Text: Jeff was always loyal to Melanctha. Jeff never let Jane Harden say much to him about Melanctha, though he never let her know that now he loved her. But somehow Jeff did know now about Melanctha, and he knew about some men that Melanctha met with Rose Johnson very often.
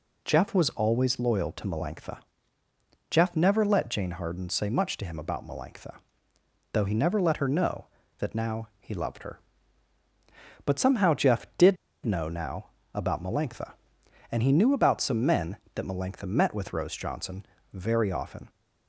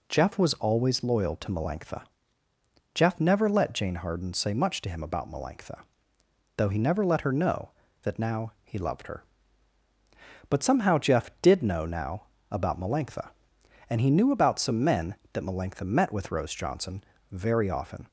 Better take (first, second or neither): second